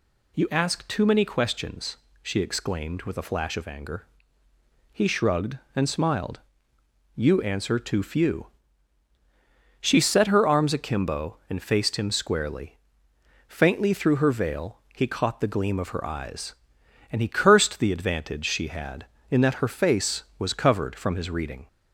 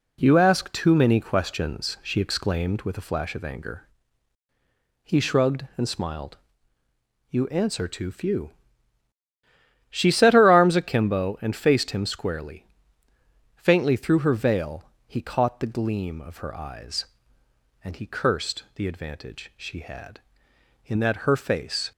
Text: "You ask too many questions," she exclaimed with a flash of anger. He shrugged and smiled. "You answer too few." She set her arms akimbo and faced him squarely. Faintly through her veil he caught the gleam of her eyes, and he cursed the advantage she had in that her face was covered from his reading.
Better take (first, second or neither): first